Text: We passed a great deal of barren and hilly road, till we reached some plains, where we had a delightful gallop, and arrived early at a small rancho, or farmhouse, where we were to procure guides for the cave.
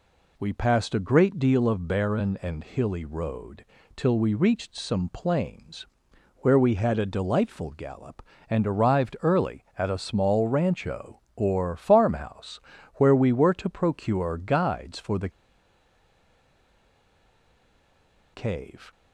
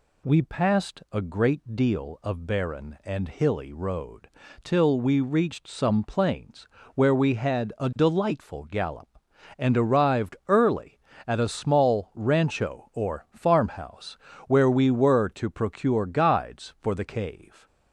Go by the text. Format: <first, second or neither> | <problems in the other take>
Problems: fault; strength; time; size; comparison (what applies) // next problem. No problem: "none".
second | pauses between "the" and "cave"; strong; at 15.2 s; 3.0 s long